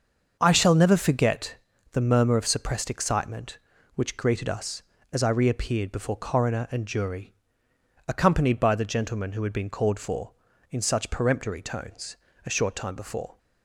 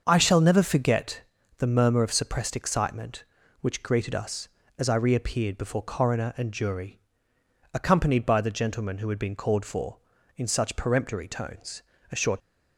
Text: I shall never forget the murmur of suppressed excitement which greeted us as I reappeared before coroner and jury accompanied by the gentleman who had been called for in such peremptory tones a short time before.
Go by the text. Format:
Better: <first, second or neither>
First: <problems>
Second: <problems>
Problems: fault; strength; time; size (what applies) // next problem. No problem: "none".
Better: first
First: starts louder than the rest; until 1.4 s; 6.5 dB // pauses between "forget" and "the"; at 1.5 s; 0.38 s long // pauses between "jury" and "accompanied"; noticeable; at 7.3 s; 0.74 s long // pauses between "tones" and "a"; slight; at 12.1 s; 0.28 s long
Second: starts louder than the rest; until 1.0 s; 6.5 dB // pauses between "forget" and "the"; at 1.2 s; 0.38 s long // pauses between "jury" and "accompanied"; noticeable; at 6.9 s; 0.74 s long // pauses between "tones" and "a"; slight; at 11.8 s; 0.28 s long // stops before "time before"; at 12.4 s